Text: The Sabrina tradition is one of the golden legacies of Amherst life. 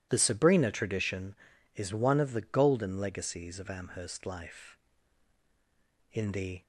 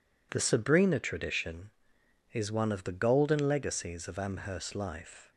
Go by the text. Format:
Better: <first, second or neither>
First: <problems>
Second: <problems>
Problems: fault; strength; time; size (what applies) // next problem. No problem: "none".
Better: second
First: goes on to say "In the"; from 6.1 s on; 0.50 s long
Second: none